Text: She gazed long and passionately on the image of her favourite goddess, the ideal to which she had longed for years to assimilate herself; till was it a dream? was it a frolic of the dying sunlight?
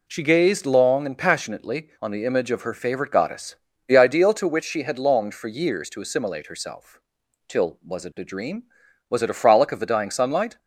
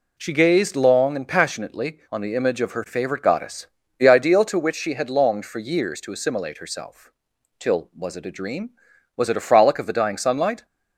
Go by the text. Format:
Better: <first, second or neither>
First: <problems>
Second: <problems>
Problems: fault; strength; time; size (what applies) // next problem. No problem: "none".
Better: neither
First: none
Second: none